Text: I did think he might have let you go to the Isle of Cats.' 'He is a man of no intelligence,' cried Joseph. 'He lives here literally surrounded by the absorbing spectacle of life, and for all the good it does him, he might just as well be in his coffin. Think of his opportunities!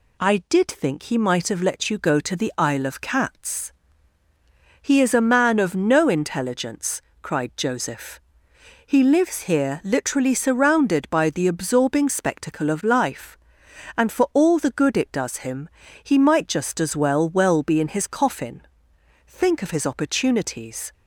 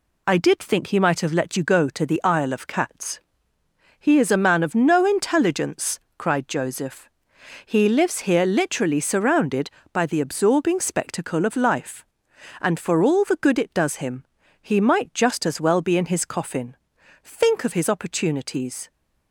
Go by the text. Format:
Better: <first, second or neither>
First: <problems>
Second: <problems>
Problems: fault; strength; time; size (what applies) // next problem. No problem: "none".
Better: second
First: says "well" twice; at 17.2 s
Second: none